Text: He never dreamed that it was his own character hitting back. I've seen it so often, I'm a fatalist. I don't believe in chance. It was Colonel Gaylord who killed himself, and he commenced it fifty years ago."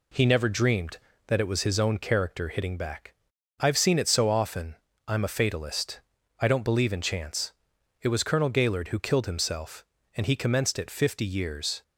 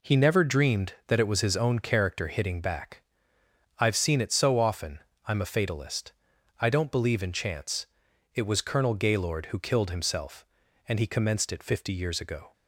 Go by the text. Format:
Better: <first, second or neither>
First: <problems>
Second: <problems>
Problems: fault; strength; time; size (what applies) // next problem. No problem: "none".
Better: second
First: stops before "ago"; at 11.8 s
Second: none